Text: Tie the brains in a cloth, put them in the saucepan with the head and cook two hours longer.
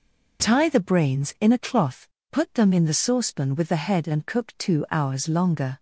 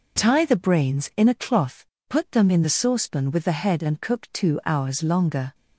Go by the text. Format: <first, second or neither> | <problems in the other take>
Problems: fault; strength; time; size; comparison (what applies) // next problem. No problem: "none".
neither | none